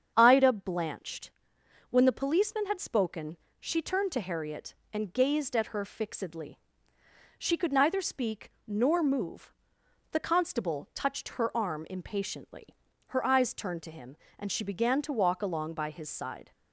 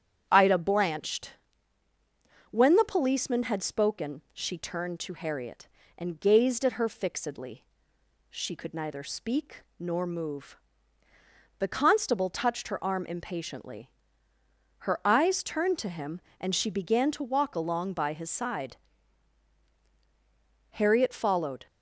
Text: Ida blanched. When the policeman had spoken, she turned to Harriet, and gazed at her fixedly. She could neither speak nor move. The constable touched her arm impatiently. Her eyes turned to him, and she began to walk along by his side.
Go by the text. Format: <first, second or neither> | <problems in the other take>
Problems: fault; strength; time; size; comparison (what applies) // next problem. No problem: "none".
first | starts louder than the rest; strong; until 1.3 s; 9 dB; strong in the first // pauses between "speak" and "nor"; slight; at 9.6 s; 0.16 s long; slight in the first // goes on to say "Harriet followed"; noticeable; from 20.7 s on; 0.96 s long